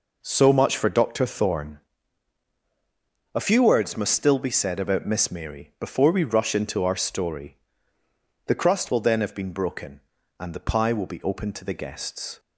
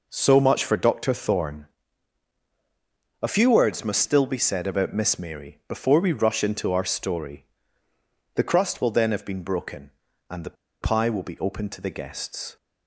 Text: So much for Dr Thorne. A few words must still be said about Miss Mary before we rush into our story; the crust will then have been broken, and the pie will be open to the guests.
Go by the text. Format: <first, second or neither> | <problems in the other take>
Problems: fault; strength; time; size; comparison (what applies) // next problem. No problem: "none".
first | pauses between "the" and "pie"; slight; at 10.5 s; 0.26 s long